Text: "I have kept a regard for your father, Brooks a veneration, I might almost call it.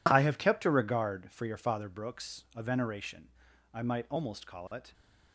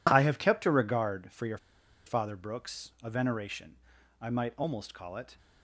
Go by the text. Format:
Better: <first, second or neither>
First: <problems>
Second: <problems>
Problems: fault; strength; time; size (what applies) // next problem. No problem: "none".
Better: first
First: none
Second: pauses between "your" and "father"; noticeable; at 1.5 s; 0.48 s long